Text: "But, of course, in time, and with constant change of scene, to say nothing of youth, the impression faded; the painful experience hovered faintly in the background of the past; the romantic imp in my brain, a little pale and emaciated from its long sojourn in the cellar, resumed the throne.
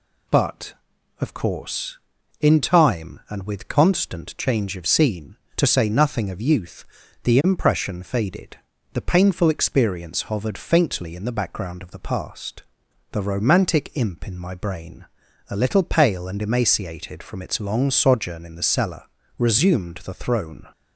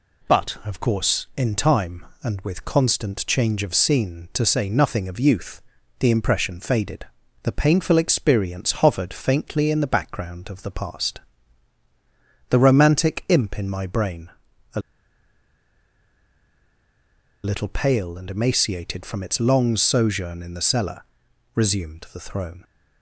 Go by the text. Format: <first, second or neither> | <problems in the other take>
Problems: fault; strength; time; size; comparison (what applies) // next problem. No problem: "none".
first | pauses between "a" and "little"; strong; at 14.8 s; 2.6 s long